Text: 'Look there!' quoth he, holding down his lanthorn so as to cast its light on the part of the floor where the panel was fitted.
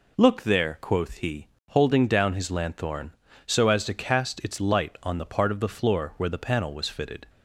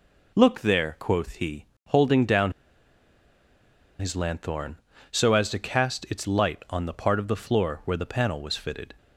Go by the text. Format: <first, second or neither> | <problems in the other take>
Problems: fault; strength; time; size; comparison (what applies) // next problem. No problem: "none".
first | pauses between "down" and "his"; strong; at 2.5 s; 1.4 s long